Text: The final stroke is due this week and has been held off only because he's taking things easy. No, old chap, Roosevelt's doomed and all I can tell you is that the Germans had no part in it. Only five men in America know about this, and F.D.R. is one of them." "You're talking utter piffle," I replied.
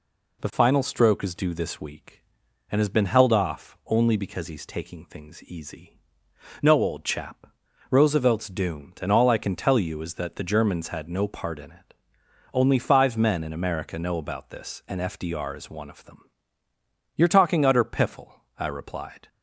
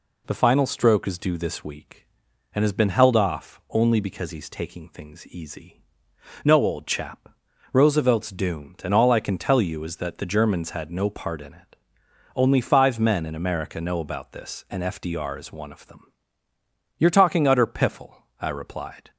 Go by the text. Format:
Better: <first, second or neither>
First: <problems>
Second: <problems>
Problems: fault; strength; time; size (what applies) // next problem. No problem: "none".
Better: neither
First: none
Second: none